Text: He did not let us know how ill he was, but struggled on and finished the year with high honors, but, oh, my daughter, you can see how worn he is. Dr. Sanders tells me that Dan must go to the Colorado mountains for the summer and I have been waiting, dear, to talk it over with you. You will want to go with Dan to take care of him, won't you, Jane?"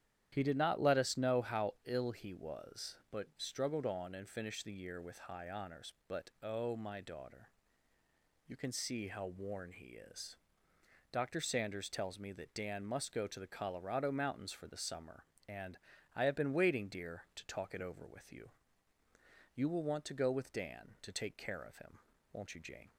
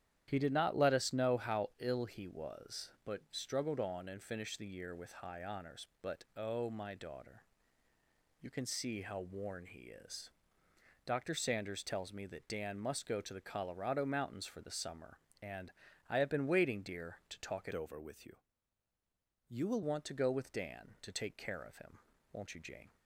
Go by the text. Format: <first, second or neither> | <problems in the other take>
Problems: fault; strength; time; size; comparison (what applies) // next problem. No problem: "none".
first | starts louder than the rest; strong; until 1.2 s; 11 dB; strong in the first // pauses between "and" and "I"; at 15.7 s; 0.40 s long; also in the first // changes voice from "over" to "will"; from 17.7 to 19.8 s; 2.1 s long